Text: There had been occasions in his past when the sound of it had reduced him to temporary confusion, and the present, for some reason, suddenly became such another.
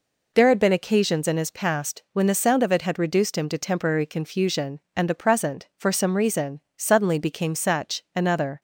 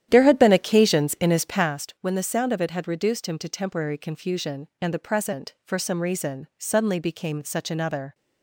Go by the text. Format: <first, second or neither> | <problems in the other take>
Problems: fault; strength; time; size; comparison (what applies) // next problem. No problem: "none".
first | starts louder than the rest; strong; until 1.8 s; 11 dB